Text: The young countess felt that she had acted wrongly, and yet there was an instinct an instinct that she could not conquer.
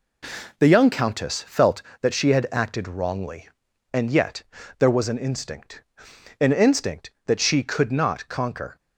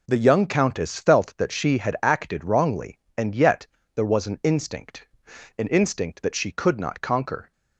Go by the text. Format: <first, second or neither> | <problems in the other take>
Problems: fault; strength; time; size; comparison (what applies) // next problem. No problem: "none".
neither | pauses between "yet" and "there"; slight; the same in both // pauses between "instinct" and "an"; noticeable; the same in both